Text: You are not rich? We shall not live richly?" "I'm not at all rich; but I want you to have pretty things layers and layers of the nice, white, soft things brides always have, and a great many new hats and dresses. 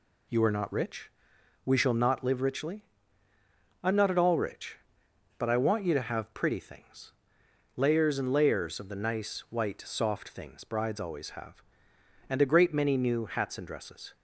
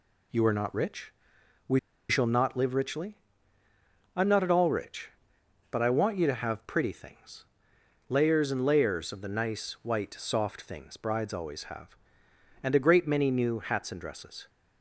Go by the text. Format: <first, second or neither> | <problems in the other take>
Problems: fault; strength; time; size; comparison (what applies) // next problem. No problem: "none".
first | pauses between "We" and "shall"; slight; at 1.7 s; 0.31 s long // pauses between "things" and "layers"; noticeable; at 7.4 s; 0.64 s long; noticeable in the first